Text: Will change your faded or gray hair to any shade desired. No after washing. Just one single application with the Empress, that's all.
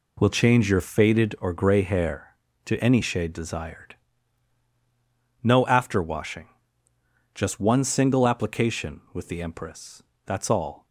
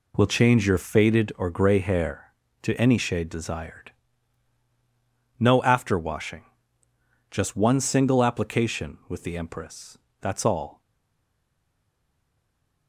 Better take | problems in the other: first | stays silent after the last word; from 10.7 s on; 2.1 s long

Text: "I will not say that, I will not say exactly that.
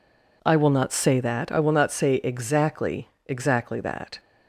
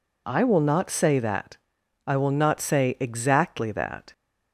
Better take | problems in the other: second | says "exactly" twice; at 3.2 s

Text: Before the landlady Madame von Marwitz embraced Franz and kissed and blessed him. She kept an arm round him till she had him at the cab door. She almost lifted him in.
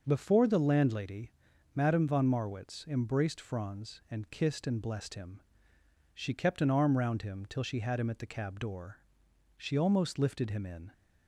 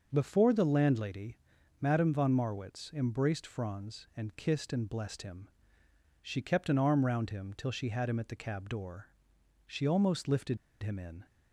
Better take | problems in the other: first | starts louder than the rest; until 1.1 s; 6 dB; noticeable in the first // pauses between "landlady" and "Madame"; noticeable; at 1.3 s; 0.46 s long; noticeable in the first // pauses between "lifted" and "him"; slight; at 10.5 s; 0.26 s long

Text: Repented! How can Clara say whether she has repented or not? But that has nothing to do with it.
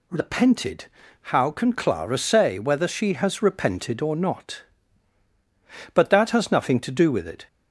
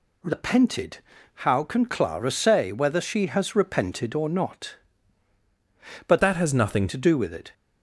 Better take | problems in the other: first | changes voice from "that" to "nothing"; from 6.2 to 6.8 s; 0.6 s long

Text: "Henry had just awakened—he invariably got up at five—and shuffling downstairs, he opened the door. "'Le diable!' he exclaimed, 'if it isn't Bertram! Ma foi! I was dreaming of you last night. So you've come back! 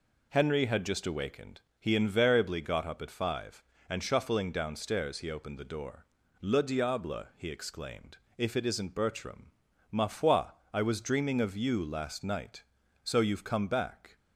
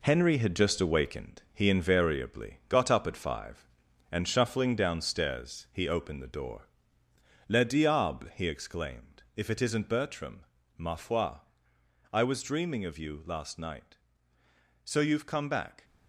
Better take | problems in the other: first | gets quieter; noticeable; throughout; 6 dB

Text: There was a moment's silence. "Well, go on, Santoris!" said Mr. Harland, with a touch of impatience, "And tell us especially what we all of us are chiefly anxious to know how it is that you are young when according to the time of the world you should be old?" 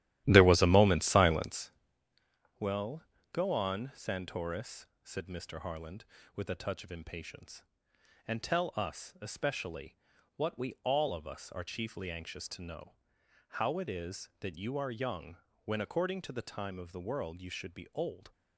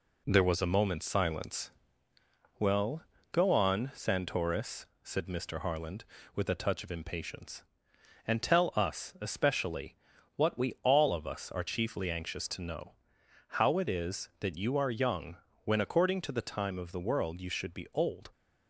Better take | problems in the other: second | starts louder than the rest; strong; until 1.7 s; 13 dB // pauses between "especially" and "what"; at 9.9 s; 0.40 s long; also in the second // pauses between "know" and "how"; noticeable; at 12.9 s; 0.64 s long; noticeable in the second // pauses between "young" and "when"; slight; at 15.3 s; 0.28 s long; slight in the second

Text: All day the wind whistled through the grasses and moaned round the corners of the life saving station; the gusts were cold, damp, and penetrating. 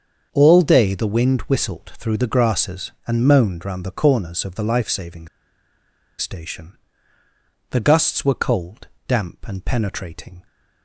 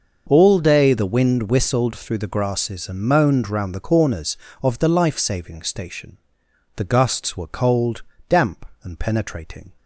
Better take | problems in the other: second | starts louder than the rest; until 1.3 s; 7 dB // pauses between "saving" and "station"; noticeable; at 5.2 s; 0.91 s long

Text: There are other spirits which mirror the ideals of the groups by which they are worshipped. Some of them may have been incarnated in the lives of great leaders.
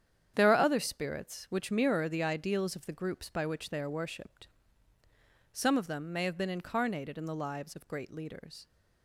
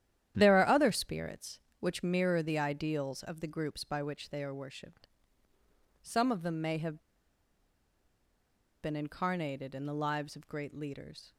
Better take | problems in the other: first | starts louder than the rest; strong; until 1.3 s; 11 dB; strong in the first // pauses between "have" and "been"; strong; at 6.9 s; 1.8 s long

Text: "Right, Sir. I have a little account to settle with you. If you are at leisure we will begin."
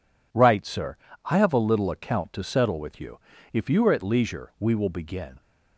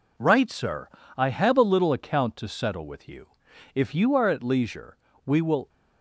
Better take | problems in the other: first | pauses between "leisure" and "we"; slight; at 4.9 s; 0.28 s long // stops before "begin"; at 5.6 s

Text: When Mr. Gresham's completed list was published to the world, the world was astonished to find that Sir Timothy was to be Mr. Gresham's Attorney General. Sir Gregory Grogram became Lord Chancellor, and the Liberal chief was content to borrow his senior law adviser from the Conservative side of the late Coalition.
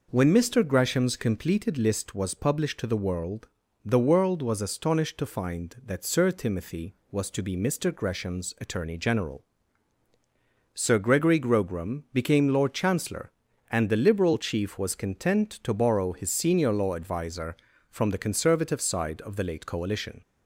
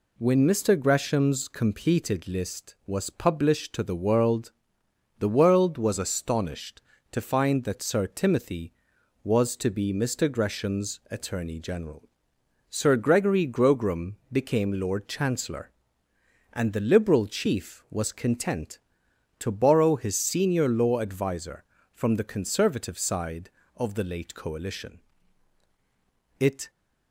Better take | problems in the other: first | pauses between "Grogram" and "became"; slight; at 14.1 s; 0.16 s long // goes on to say "It"; slight; from 26.3 s on; 0.30 s long

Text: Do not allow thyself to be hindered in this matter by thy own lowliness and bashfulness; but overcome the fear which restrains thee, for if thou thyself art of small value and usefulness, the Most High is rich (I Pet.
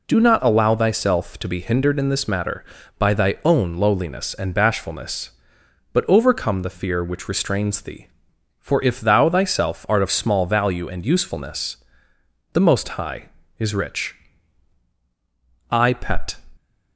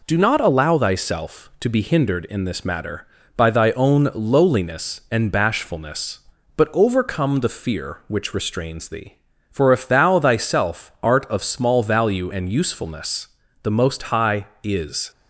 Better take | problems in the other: first | stops before "rich I Pet"; at 15.1 s

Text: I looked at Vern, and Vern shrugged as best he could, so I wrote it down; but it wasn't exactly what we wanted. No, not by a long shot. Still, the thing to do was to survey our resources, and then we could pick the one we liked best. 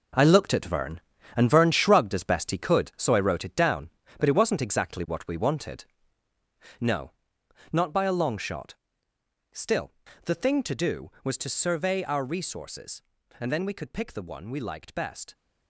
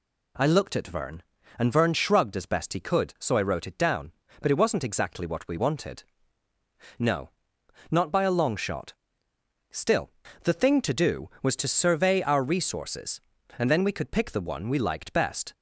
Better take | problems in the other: second | gets quieter; strong; throughout; 10 dB

